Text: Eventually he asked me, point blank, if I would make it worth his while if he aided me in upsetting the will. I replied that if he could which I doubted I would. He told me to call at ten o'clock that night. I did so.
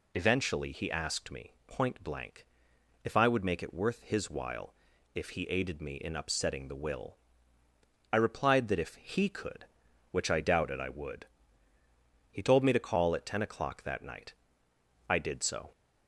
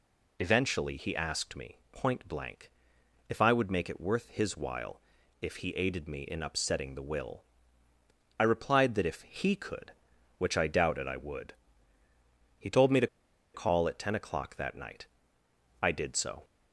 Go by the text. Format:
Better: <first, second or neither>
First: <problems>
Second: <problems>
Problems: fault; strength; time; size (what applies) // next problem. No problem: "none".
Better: first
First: pauses between "while" and "if"; at 4.7 s; 0.40 s long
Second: pauses between "while" and "if"; at 5.0 s; 0.40 s long // pauses between "to" and "call"; noticeable; at 13.0 s; 0.47 s long